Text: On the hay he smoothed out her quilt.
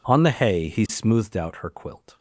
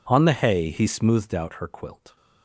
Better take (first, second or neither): neither